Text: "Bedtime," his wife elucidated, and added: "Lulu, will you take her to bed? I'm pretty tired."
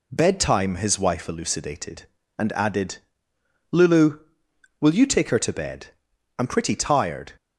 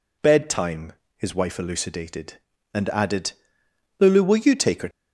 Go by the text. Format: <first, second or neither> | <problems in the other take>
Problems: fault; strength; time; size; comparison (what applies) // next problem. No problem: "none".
first | stops before "to bed I'm pretty tired"; at 4.9 s